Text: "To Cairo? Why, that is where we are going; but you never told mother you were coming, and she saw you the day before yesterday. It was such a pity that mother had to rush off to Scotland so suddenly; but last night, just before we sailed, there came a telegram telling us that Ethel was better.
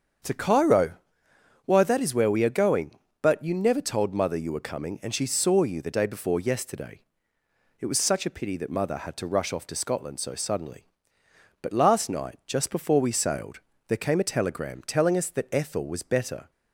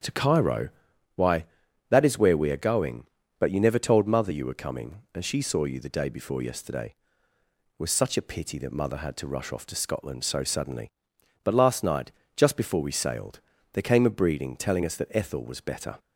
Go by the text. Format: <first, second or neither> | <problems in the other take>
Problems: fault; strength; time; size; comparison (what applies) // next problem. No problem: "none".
first | starts louder than the rest; strong; until 1.9 s; 8.5 dB; strong in the first // says "breeding" for "telegram"; at 14.1 s